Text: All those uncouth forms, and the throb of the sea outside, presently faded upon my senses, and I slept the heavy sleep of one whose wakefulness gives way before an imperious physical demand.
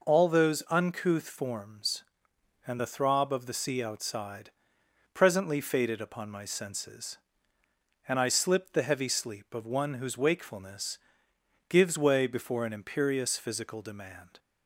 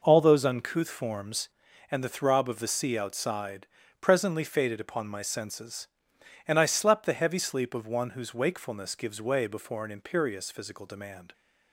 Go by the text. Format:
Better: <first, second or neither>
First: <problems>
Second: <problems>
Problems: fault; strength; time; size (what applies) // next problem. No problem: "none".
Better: second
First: says "slipped" for "slept"; at 8.2 s // pauses between "wakefulness" and "gives"; noticeable; at 10.9 s; 0.72 s long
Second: none